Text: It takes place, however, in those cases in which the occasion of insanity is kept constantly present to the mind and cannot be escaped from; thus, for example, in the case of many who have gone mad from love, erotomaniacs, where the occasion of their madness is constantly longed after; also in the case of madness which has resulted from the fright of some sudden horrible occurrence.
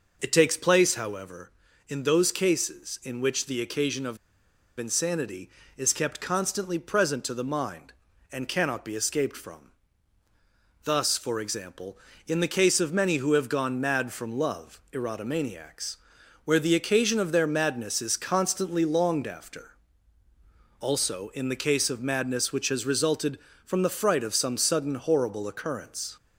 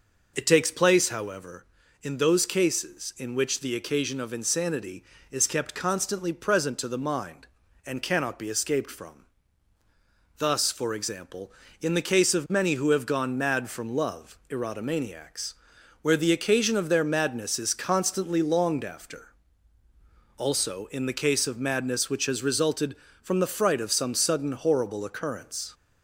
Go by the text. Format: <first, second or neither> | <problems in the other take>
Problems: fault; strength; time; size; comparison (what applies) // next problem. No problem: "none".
second | pauses between "of" and "insanity"; noticeable; at 4.1 s; 0.60 s long